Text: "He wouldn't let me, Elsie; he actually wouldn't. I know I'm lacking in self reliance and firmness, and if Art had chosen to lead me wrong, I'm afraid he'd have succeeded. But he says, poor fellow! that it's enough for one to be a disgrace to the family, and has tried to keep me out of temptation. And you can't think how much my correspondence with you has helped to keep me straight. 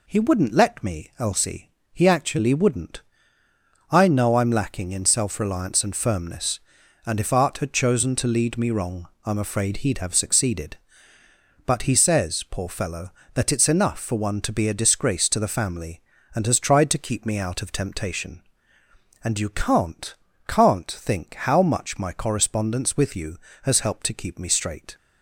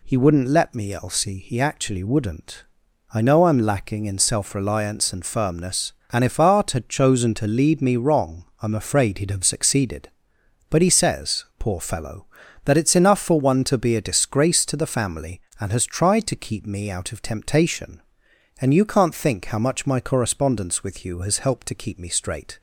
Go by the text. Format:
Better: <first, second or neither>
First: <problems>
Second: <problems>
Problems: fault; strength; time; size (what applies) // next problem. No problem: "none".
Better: second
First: says "can't" twice; at 20.4 s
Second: none